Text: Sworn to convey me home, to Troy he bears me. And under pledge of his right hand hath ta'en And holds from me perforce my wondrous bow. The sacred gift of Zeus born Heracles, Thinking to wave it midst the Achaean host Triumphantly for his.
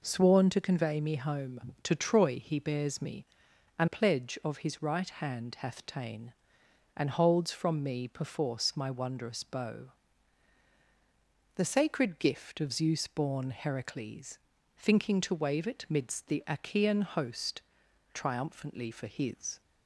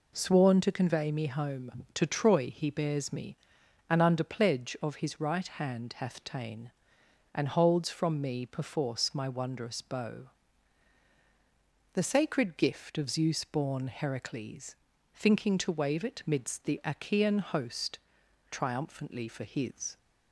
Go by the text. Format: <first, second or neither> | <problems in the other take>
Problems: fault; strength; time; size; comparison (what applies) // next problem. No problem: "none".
second | skips "under"; at 3.8 s // pauses between "host" and "Triumphantly"; noticeable; at 17.5 s; 0.54 s long; noticeable in the second